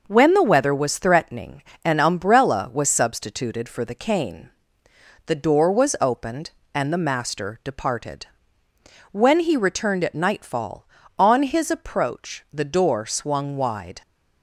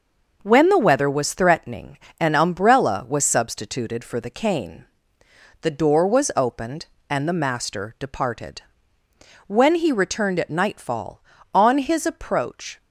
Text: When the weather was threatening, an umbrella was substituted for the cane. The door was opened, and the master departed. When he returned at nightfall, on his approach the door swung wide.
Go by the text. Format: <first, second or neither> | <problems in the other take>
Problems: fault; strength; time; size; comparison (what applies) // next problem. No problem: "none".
first | stops before "the door swung wide"; at 12.8 s